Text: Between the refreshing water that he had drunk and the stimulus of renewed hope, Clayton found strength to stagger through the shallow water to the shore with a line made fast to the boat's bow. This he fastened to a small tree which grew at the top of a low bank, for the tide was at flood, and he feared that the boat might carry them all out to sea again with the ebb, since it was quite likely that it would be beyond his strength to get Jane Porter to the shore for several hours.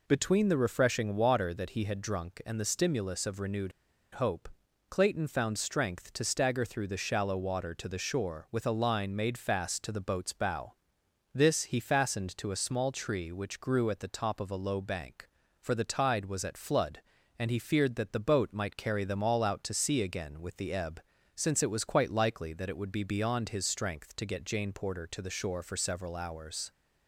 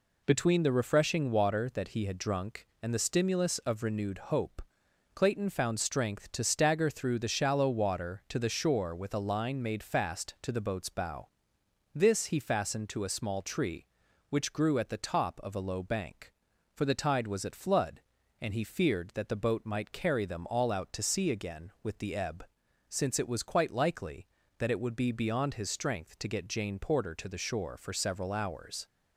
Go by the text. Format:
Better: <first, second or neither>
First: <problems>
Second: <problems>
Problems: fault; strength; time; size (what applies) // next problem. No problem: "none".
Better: second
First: pauses between "renewed" and "hope"; at 3.7 s; 0.41 s long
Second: none